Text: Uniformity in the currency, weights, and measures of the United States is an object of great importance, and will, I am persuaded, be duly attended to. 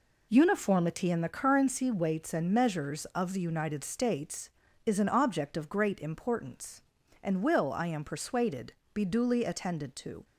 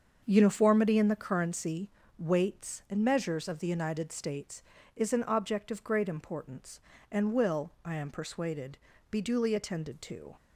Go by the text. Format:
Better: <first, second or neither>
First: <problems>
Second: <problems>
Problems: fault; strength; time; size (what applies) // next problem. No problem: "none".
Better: first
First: none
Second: starts louder than the rest; until 1.4 s; 7 dB